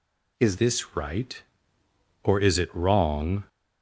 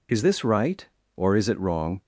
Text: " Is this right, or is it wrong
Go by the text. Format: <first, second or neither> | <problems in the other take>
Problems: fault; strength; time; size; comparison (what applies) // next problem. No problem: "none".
second | changes voice at "this"; from 0.5 s on; 2.9 s long